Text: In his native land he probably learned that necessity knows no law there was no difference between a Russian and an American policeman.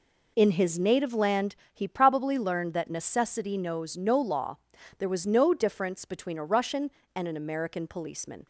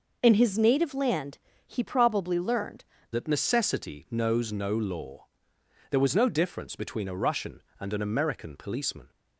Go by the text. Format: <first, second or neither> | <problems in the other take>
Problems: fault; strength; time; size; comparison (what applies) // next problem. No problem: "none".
first | pauses between "land" and "he"; slight; at 1.3 s; 0.28 s long; slight in the first // changes voice at "that"; from 3.1 s on; 6.0 s long // pauses between "law" and "there"; noticeable; at 5.2 s; 0.64 s long; also in the first